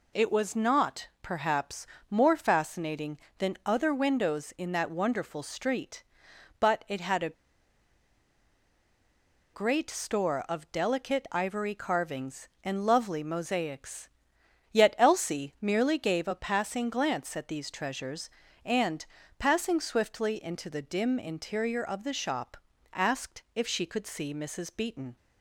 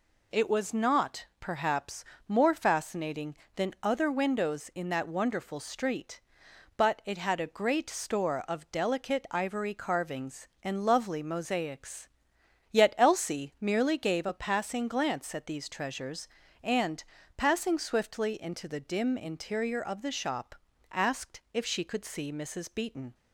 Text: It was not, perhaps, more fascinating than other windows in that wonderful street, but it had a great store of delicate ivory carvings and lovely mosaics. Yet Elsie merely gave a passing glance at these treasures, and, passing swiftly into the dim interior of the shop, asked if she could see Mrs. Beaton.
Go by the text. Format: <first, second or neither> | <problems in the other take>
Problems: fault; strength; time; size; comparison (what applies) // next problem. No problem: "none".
second | pauses between "a" and "great"; strong; at 7.3 s; 2.2 s long